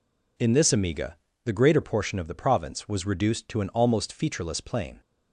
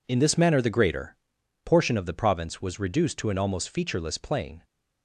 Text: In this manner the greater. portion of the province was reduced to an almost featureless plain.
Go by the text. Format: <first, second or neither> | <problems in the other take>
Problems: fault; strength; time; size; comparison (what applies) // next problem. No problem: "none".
second | says "amiga" for "manner"; at 0.7 s